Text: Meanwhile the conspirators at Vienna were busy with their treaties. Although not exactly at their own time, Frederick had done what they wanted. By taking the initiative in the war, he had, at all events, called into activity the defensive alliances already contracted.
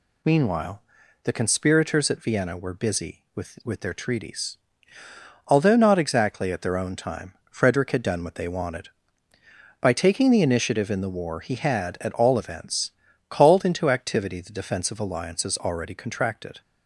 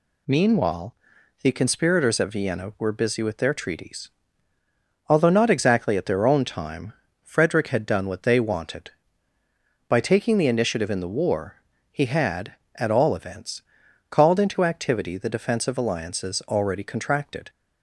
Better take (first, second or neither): second